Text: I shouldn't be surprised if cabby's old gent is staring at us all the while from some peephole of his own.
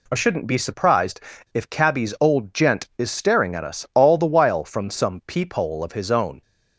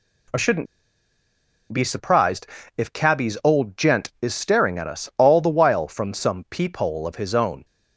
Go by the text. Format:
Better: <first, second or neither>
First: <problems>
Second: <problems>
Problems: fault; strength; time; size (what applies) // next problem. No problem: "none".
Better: first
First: pauses between "surprised" and "if"; slight; at 1.1 s; 0.34 s long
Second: pauses between "shouldn't" and "be"; at 0.6 s; 1.0 s long // pauses between "surprised" and "if"; slight; at 2.4 s; 0.32 s long